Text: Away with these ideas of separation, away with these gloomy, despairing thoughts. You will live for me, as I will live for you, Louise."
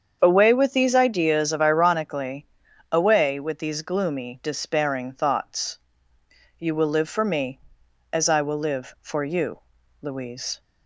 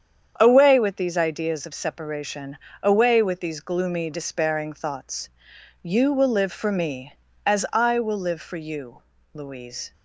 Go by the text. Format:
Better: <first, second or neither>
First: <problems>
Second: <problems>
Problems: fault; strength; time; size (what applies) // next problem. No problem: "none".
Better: second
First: starts louder than the rest; strong; until 1.2 s; 7.5 dB // says "ironically" for "separation"; at 1.6 s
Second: starts louder than the rest; strong; until 1.3 s; 8 dB